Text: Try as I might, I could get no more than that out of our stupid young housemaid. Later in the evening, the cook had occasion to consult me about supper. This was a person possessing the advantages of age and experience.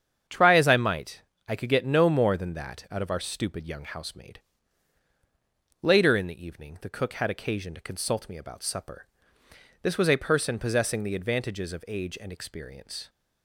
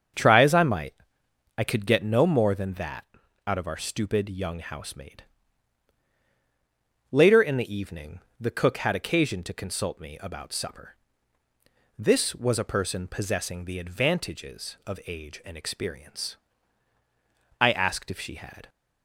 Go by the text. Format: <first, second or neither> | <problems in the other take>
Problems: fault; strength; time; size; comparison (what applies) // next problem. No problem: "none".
first | starts louder than the rest; strong; until 1.8 s; 7 dB; strong in the first // pauses between "that" and "out"; at 3.0 s; 0.42 s long // goes on to say "I asked if she had"; noticeable; from 17.6 s on; 1.0 s long